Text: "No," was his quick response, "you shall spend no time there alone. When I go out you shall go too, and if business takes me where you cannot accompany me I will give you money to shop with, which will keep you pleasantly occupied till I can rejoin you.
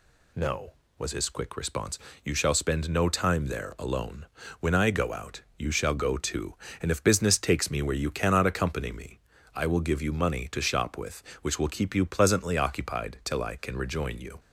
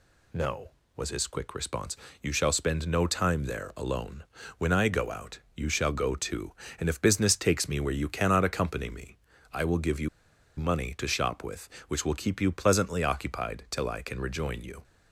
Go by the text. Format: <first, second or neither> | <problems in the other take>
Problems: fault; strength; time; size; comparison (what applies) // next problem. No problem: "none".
first | pauses between "out" and "you"; slight; at 5.4 s; 0.16 s long; slight in the first // pauses between "me" and "I"; slight; at 9.1 s; 0.34 s long; slight in the first // pauses between "you" and "money"; noticeable; at 10.0 s; 0.48 s long